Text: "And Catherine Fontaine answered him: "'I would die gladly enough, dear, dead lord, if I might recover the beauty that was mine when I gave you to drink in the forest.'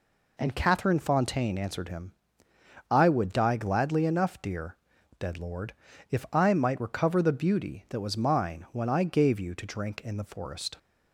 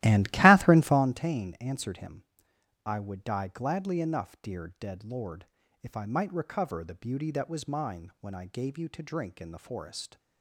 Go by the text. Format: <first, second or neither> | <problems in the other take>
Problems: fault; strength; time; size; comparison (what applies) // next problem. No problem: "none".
first | starts louder than the rest; strong; until 1.2 s; 15 dB